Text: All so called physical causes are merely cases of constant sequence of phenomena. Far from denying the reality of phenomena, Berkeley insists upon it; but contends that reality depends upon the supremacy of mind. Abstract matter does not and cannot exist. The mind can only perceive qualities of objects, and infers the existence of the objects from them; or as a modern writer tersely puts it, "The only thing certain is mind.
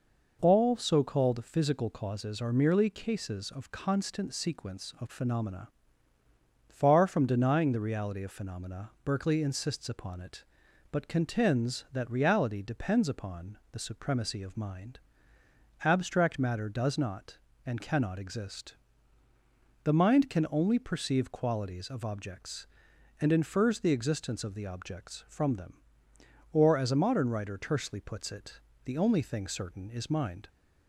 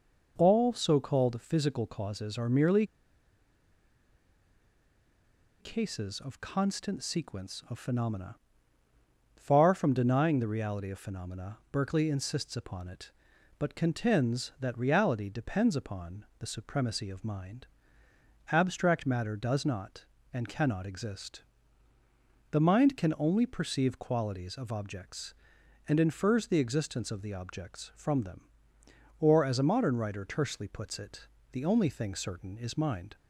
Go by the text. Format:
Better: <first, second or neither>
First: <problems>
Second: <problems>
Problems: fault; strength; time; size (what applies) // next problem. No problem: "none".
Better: first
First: none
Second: pauses between "merely" and "cases"; strong; at 2.8 s; 2.7 s long